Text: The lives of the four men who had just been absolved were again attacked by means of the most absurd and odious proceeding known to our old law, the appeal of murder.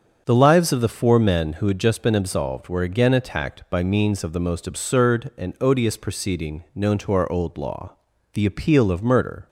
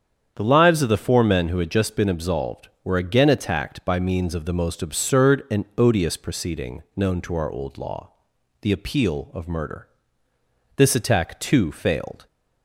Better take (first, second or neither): first